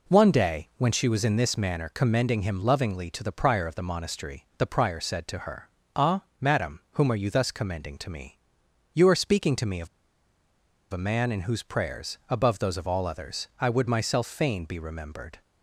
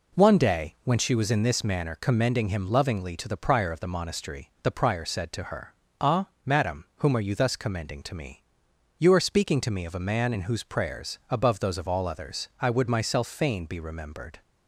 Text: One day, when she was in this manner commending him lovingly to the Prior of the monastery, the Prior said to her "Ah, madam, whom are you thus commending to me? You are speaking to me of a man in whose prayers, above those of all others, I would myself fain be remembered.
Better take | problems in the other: second | pauses between "her" and "Ah"; slight; at 5.6 s; 0.30 s long; slight in the second // pauses between "of" and "a"; at 9.8 s; 1.0 s long

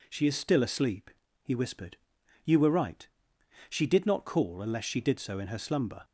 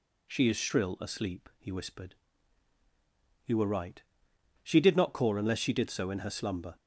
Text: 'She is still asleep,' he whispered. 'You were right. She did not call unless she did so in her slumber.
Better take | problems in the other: first | says "shrill" for "still"; at 0.5 s

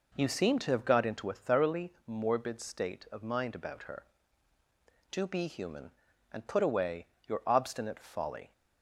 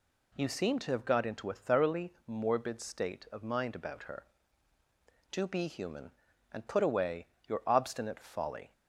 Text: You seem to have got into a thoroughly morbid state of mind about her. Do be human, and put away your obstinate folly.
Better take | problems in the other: second | starts louder than the rest; noticeable; until 1.4 s; 4.5 dB // pauses between "thoroughly" and "morbid"; slight; at 1.8 s; 0.16 s long; slight in the second // pauses between "away" and "your"; slight; at 7.0 s; 0.22 s long; slight in the second

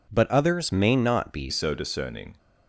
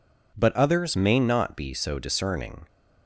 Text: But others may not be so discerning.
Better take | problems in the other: second | changes voice at "so"; from 1.4 s on; 0.9 s long

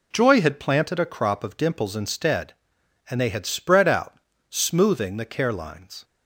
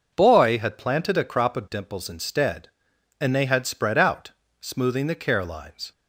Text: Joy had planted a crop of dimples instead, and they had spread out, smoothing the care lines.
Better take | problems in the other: first | says "Boy" for "Joy"; at 0.1 s

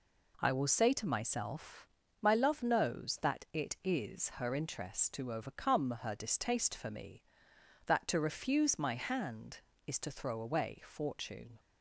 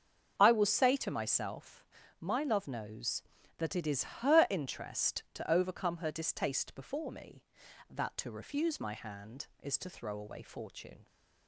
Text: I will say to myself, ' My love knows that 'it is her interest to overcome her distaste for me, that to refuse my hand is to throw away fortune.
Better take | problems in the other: first | starts louder than the rest; until 1.3 s; 6.5 dB // says "before" for "for"; at 6.7 s

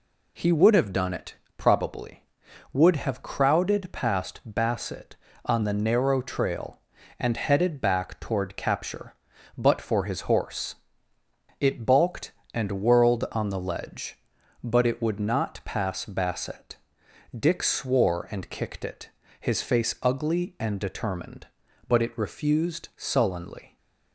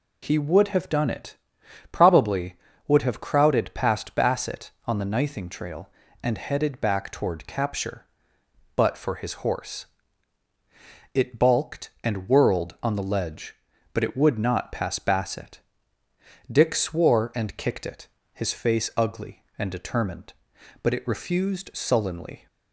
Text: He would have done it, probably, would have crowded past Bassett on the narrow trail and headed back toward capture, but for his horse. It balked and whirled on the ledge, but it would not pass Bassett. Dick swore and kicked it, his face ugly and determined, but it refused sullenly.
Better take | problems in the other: first | says "nything" for "narrow"; at 5.0 s

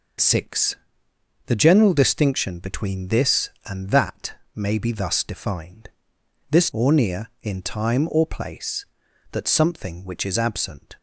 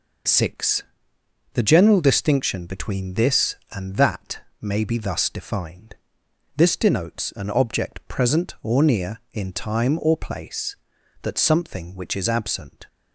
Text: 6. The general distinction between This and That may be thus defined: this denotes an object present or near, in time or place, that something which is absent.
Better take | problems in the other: second | pauses between "That" and "may"; slight; at 4.3 s; 0.18 s long; slight in the second // skips "denotes an object present"; at 6.7 s

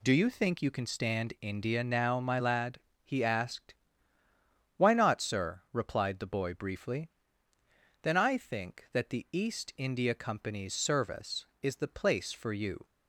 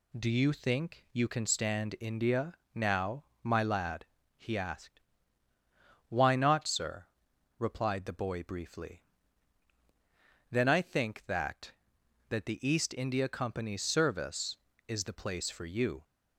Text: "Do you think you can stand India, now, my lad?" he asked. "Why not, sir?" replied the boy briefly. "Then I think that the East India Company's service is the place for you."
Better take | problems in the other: first | says "that" twice; at 12.2 s

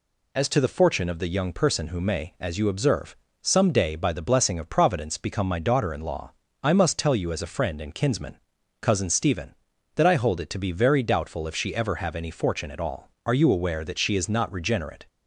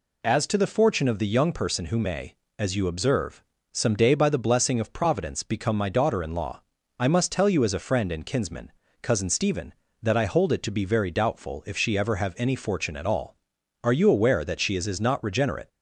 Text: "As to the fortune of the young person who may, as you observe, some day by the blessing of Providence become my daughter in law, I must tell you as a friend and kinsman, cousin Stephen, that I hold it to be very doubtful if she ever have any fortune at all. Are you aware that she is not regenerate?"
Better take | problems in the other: first | says "is" twice; at 14.8 s

